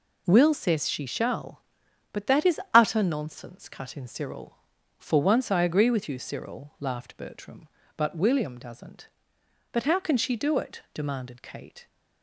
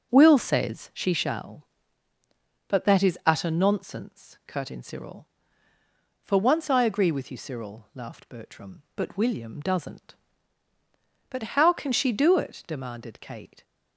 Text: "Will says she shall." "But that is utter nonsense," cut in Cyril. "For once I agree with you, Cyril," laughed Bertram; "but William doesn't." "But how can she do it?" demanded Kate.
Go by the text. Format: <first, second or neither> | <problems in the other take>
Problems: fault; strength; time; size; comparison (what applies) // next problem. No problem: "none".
first | starts louder than the rest; noticeable; until 1.1 s; 6 dB